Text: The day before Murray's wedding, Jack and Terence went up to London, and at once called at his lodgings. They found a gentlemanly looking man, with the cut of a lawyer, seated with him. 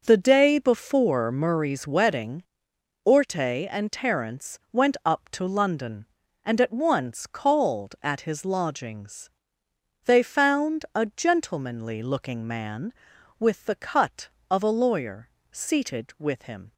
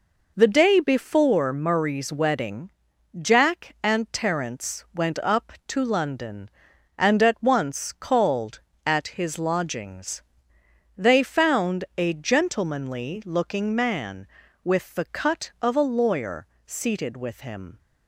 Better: second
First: starts louder than the rest; noticeable; until 1.0 s; 6 dB // says "Orte" for "Jack"; at 3.0 s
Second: none

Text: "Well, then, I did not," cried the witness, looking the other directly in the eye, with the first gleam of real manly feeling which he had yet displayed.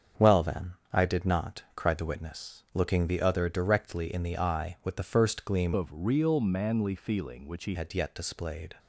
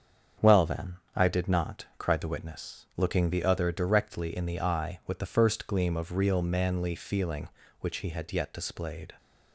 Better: second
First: starts louder than the rest; strong; until 1.3 s; 7.5 dB // changes voice from "of" to "he"; from 5.7 to 7.7 s; 2.0 s long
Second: starts louder than the rest; strong; until 1.5 s; 7.5 dB

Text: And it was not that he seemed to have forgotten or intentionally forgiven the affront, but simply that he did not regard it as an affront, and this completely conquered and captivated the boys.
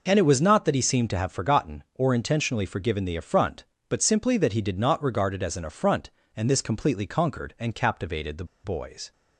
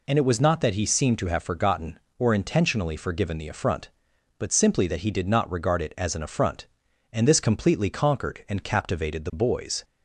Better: second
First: pauses between "the" and "boys"; slight; at 8.4 s; 0.19 s long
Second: none

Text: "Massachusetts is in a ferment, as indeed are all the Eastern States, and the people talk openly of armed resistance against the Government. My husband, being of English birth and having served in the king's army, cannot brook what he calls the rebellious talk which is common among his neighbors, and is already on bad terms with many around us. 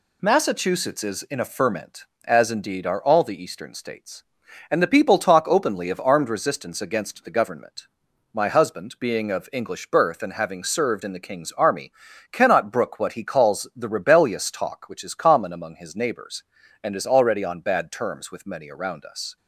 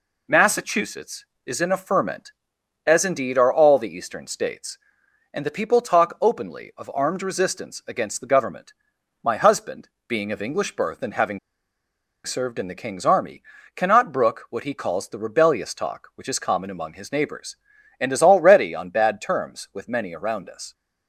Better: first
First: none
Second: pauses between "having" and "served"; noticeable; at 11.3 s; 0.85 s long

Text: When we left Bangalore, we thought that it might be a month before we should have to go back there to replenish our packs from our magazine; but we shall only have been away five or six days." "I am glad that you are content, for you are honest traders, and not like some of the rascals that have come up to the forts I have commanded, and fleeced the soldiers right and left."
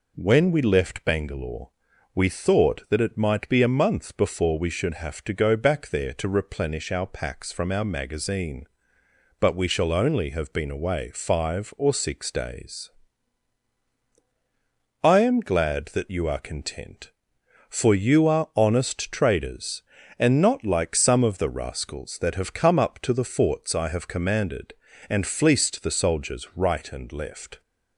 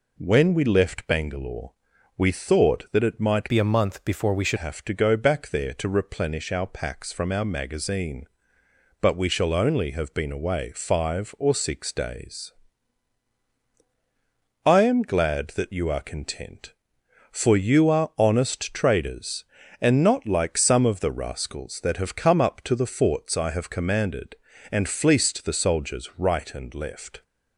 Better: first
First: none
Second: changes voice from "be" to "should"; from 3.4 to 4.5 s; 1.1 s long

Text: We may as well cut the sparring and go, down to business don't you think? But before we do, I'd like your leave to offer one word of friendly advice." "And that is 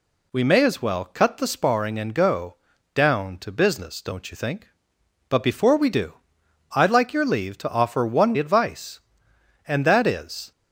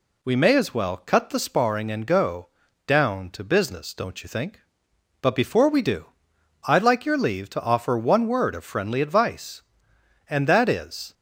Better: second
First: skips "word of friendly"; at 8.3 s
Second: none

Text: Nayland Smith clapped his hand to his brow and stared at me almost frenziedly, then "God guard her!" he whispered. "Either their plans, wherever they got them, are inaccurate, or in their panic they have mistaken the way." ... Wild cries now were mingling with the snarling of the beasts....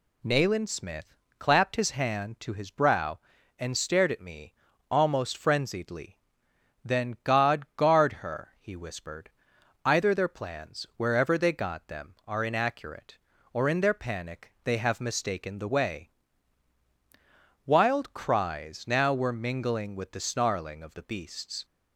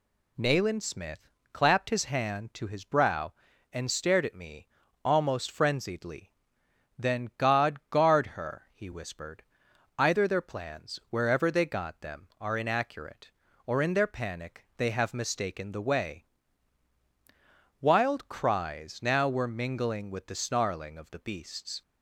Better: neither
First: pauses between "Smith" and "clapped"; slight; at 1.1 s; 0.22 s long // pauses between "me" and "almost"; slight; at 4.5 s; 0.36 s long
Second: pauses between "Smith" and "clapped"; slight; at 1.3 s; 0.22 s long // pauses between "me" and "almost"; slight; at 4.6 s; 0.36 s long

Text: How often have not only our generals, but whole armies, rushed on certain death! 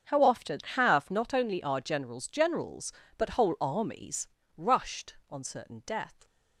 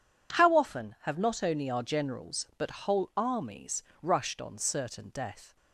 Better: second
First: starts louder than the rest; strong; until 1.2 s; 7 dB // says "generals" twice; at 2.2 s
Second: none

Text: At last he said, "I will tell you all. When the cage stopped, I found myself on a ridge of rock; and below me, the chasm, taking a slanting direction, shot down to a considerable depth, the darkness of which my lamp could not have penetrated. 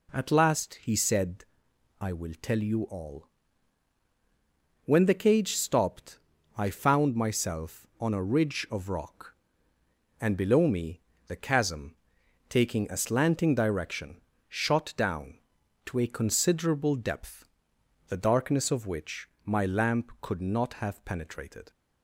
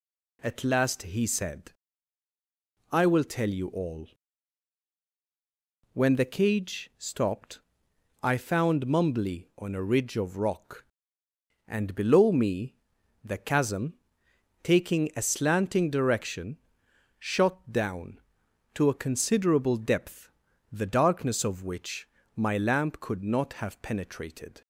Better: first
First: pauses between "which" and "my"; slight; at 19.2 s; 0.18 s long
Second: says "mumbly" for "myself"; at 8.8 s // pauses between "which" and "my"; slight; at 22.0 s; 0.30 s long

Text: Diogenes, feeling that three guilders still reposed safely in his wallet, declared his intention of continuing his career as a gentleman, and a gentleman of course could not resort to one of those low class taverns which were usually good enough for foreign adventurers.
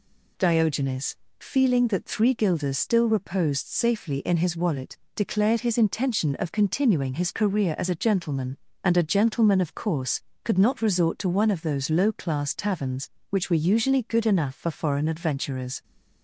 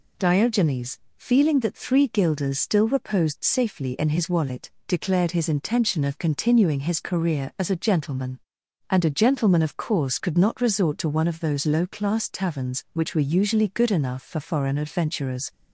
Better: neither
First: none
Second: none

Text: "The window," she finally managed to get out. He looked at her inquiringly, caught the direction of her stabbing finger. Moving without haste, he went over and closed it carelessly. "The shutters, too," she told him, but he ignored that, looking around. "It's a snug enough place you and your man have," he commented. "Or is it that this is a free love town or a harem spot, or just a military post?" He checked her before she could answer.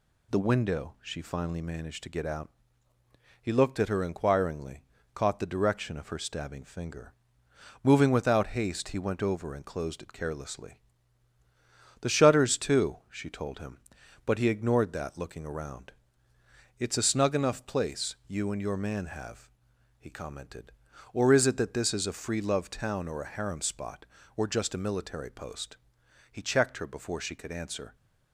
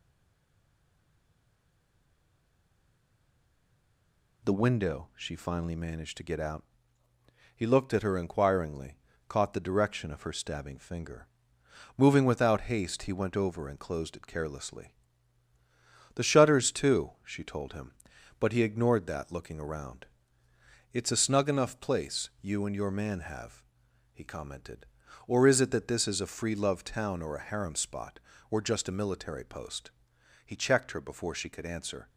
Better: first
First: none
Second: stays silent before the first word; strong; until 4.4 s; 4.4 s long

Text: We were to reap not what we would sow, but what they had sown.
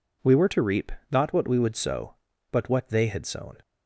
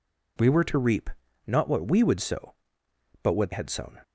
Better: first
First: pauses between "reap" and "not"; slight; at 0.9 s; 0.20 s long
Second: pauses between "reap" and "not"; at 1.0 s; 0.38 s long // skips "they"; at 3.5 s

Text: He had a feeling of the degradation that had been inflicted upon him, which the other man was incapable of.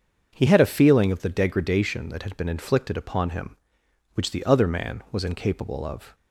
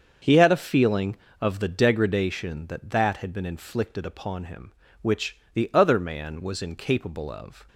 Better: first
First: starts louder than the rest; until 1.3 s; 7 dB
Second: starts louder than the rest; until 1.4 s; 7 dB // says "that" twice; at 2.9 s // pauses between "which" and "the"; slight; at 5.3 s; 0.18 s long

